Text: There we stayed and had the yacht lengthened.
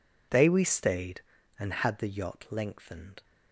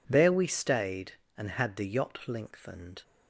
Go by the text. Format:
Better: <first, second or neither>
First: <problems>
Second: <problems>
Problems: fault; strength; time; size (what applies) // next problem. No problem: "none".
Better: second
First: says "They" for "There"; at 0.3 s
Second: none